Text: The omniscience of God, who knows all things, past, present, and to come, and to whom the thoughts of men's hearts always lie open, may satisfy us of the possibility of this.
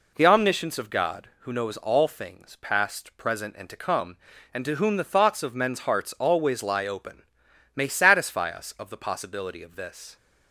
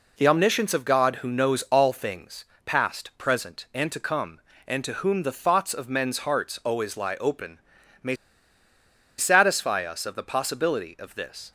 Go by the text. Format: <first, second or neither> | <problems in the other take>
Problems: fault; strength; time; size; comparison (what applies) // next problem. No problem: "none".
first | pauses between "may" and "satisfy"; at 8.1 s; 1.0 s long